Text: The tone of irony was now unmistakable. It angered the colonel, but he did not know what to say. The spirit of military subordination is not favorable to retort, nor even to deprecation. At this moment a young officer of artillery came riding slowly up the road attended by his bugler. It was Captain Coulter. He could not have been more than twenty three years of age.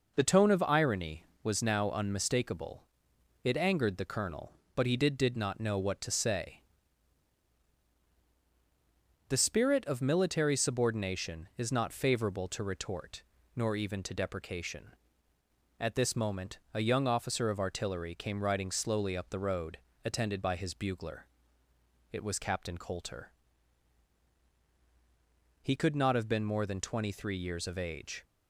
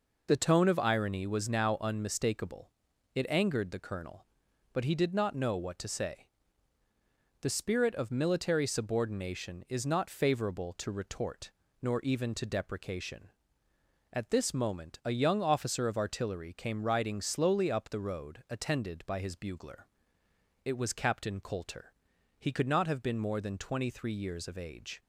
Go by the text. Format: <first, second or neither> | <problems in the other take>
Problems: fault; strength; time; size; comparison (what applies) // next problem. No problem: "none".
second | says "did" twice; at 5.1 s // pauses between "road" and "attended"; slight; at 19.7 s; 0.28 s long